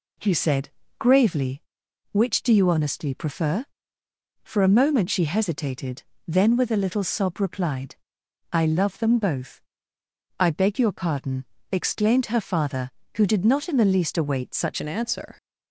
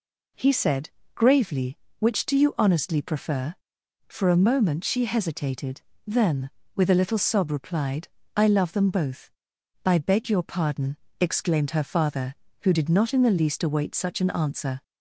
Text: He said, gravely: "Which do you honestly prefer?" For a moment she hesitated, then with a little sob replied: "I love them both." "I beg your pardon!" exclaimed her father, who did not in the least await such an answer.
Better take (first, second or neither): second